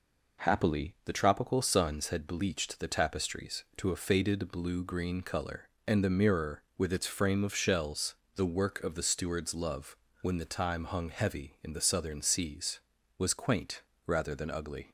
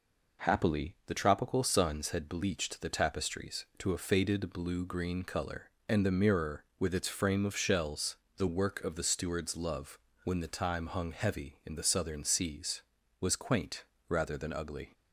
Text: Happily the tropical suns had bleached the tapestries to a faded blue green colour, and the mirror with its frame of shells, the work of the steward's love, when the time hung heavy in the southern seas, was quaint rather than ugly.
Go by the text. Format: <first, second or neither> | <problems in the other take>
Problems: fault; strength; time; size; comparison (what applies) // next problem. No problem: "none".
neither | pauses between "quaint" and "rather"; slight; the same in both